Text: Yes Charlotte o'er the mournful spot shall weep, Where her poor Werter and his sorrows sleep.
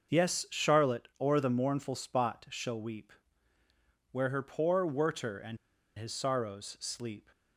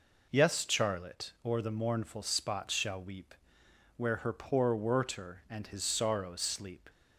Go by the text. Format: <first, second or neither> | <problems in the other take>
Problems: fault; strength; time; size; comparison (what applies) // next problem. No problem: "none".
second | starts louder than the rest; until 1.2 s; 6 dB // pauses between "and" and "his"; at 5.5 s; 0.40 s long